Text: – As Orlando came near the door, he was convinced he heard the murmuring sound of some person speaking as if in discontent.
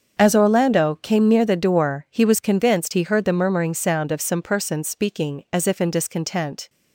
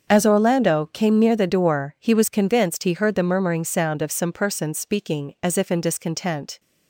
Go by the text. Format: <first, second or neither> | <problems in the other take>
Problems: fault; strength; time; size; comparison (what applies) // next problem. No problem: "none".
neither | starts louder than the rest; the same in both